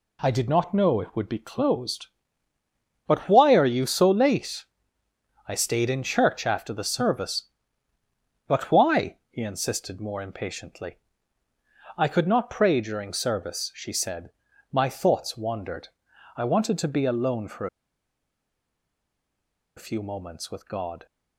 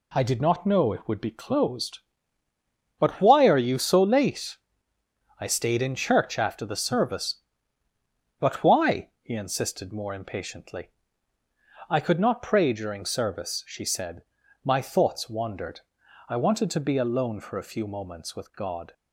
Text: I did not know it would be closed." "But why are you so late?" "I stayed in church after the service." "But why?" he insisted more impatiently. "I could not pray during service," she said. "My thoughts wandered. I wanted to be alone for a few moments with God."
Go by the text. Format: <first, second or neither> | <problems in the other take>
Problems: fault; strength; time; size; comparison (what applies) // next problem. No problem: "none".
second | pauses between "for" and "a"; strong; at 17.6 s; 2.1 s long